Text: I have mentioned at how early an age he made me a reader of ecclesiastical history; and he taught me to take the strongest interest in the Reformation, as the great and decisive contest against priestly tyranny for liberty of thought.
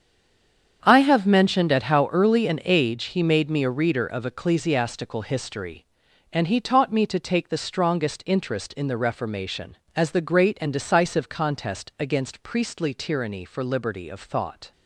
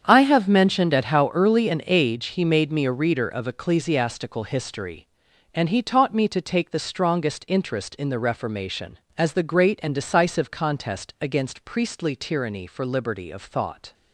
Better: second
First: stays silent before the first word; slight; until 0.8 s; 0.8 s long // starts louder than the rest; strong; until 1.8 s; 8 dB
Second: starts louder than the rest; strong; until 1.0 s; 8 dB

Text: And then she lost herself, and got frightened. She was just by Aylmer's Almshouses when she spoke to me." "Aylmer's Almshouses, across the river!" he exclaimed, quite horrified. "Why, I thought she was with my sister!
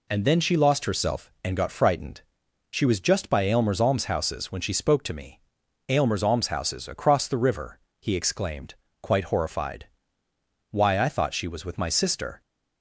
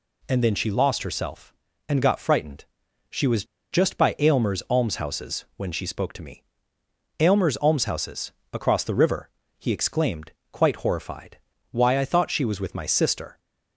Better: first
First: none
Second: pauses between "was" and "just"; slight; at 3.4 s; 0.27 s long

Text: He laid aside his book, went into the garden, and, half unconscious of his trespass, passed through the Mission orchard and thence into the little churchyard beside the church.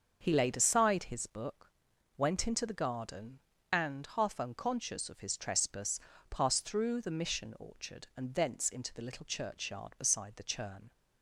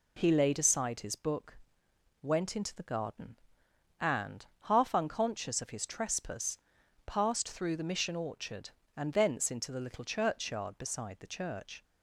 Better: second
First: starts louder than the rest; until 1.2 s; 6.5 dB // says "churn" for "church"; at 10.4 s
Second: none

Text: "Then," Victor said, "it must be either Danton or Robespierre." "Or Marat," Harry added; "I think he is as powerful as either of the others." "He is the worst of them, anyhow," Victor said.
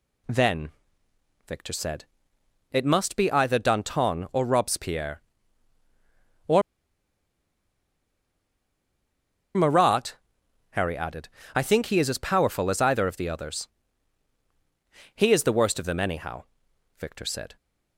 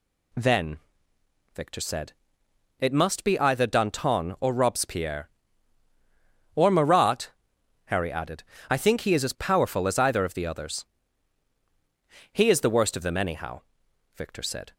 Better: second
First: pauses between "Or" and "Marat"; strong; at 6.6 s; 2.9 s long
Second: none

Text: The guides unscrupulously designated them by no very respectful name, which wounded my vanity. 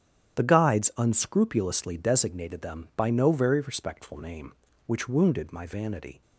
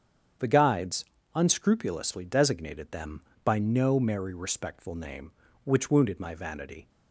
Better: first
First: starts louder than the rest; strong; until 1.4 s; 9 dB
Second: starts louder than the rest; strong; until 1.7 s; 7.5 dB // pauses between "guides" and "unscrupulously"; slight; at 1.0 s; 0.32 s long // says "merry" for "very"; at 3.9 s

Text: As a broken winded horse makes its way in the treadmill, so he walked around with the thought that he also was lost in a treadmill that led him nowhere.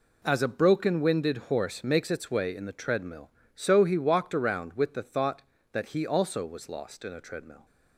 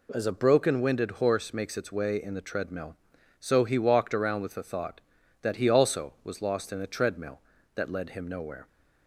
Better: second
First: stops before "that led him nowhere"; at 7.6 s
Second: none

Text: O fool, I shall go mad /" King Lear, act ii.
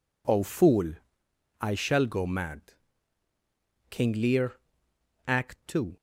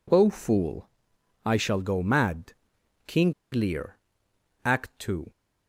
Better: first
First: none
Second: pauses between "King" and "Lear"; slight; at 3.3 s; 0.19 s long

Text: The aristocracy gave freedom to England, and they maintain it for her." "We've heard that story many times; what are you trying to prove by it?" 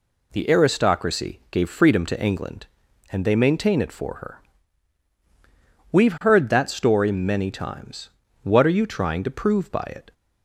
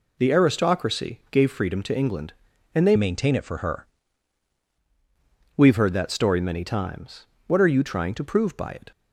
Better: first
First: none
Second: changes voice from "maintain" to "her"; from 2.9 to 3.8 s; 0.9 s long

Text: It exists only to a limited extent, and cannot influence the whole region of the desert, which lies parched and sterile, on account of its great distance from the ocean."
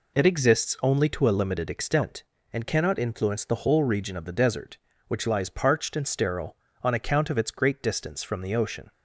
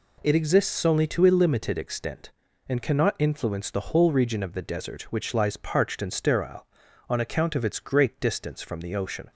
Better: neither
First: none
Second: none

